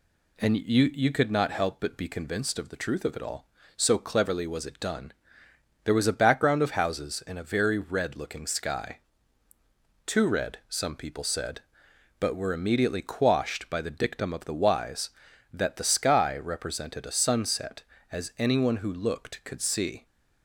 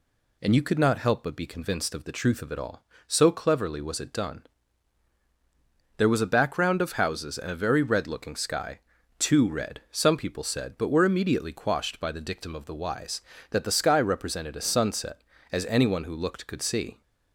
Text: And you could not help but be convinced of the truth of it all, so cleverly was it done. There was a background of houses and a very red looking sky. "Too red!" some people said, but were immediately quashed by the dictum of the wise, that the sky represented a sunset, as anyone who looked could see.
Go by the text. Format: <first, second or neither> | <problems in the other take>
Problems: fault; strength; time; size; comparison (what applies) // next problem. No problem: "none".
second | says "you" twice; at 0.9 s